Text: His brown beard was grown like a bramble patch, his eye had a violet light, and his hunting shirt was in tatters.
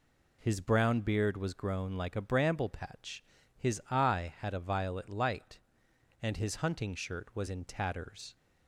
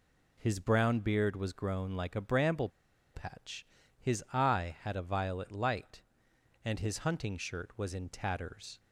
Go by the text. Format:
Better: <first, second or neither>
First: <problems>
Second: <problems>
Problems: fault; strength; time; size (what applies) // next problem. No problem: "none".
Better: first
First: none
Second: pauses between "bramble" and "patch"; at 2.6 s; 0.45 s long